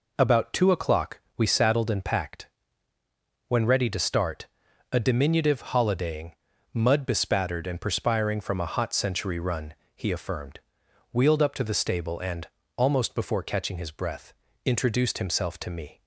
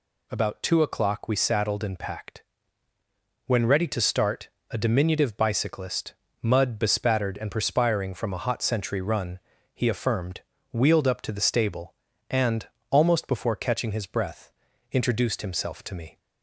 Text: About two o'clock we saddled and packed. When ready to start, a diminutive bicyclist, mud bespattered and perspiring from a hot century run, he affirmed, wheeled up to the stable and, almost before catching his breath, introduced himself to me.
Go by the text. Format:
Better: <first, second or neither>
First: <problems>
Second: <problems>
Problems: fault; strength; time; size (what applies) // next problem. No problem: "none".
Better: second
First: pauses between "o'clock" and "we"; slight; at 1.1 s; 0.16 s long // says "holidaying" for "bicyclist"; at 5.5 s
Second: none